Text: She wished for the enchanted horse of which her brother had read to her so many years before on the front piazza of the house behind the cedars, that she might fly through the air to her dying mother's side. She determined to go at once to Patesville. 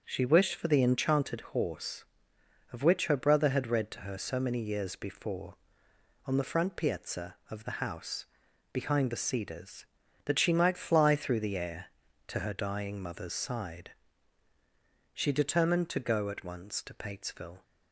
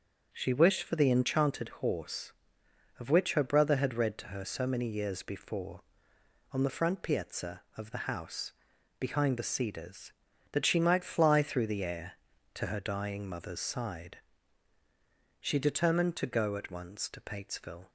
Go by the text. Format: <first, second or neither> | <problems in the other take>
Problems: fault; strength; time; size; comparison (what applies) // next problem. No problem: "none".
neither | pauses between "house" and "behind"; noticeable; the same in both